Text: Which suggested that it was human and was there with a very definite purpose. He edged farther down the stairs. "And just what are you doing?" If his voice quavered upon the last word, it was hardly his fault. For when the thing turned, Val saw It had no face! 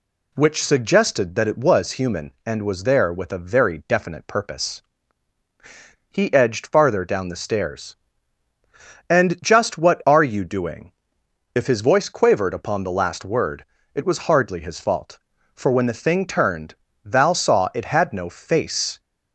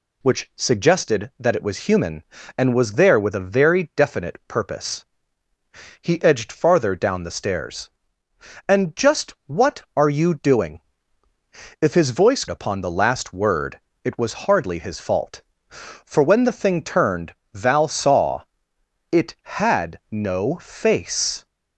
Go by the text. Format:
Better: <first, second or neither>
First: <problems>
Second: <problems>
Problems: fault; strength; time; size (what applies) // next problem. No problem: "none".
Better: first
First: none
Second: skips "quavered"; at 12.4 s // pauses between "saw" and "It"; noticeable; at 18.4 s; 0.66 s long